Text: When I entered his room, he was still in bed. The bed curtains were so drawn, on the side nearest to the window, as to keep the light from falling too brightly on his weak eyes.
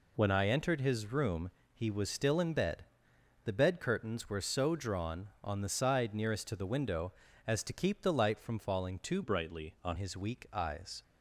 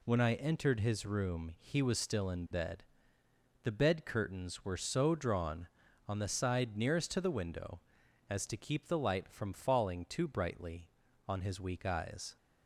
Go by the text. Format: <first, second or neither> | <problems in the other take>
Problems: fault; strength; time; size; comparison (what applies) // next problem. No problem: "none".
second | changes voice from "brightly" to "on"; from 9.2 to 9.9 s; 0.7 s long